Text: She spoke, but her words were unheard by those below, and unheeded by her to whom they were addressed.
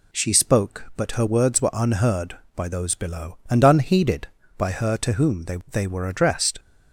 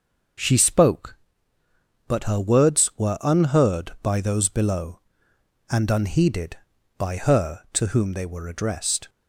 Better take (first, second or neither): second